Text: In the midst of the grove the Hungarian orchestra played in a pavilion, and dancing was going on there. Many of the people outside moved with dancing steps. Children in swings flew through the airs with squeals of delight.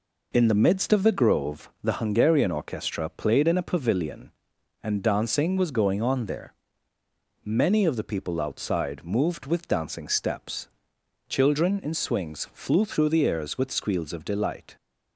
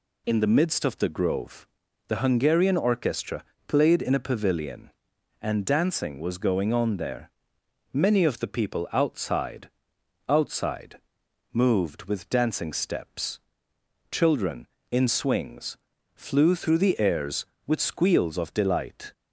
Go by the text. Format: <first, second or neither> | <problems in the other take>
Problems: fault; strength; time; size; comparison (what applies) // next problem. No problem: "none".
first | pauses between "grove" and "the"; at 1.6 s; 0.42 s long; slight in the first // pauses between "orchestra" and "played"; slight; at 3.4 s; 0.24 s long // says "outside" twice; at 10.2 s // pauses between "swings" and "flew"; slight; at 15.7 s; 0.36 s long